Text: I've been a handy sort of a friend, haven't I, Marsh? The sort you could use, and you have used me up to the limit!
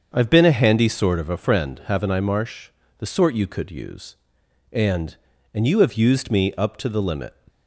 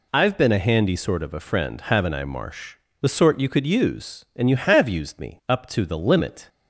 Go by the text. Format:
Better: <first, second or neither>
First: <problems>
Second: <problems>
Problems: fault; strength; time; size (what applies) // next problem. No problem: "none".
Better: second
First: starts louder than the rest; until 1.1 s; 6.5 dB // says "and" twice; at 5.5 s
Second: none